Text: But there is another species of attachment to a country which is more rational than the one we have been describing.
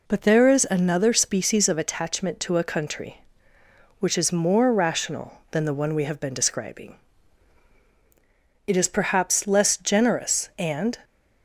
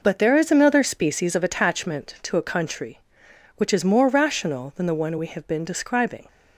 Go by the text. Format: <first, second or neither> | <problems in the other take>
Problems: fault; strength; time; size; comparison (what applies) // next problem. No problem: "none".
second | goes on to say "It is perhaps less generous and"; strong; from 8.6 s on; 2.3 s long